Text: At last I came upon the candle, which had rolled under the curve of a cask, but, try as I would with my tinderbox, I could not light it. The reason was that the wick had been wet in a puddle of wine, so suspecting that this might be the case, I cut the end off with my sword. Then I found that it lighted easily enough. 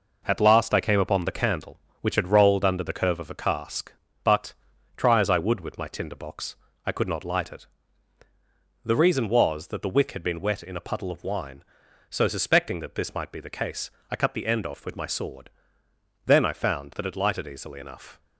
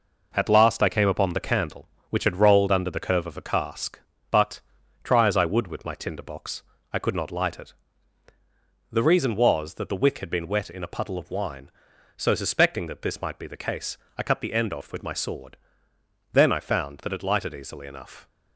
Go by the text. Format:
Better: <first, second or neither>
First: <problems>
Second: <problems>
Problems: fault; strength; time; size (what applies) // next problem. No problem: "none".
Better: neither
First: none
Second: none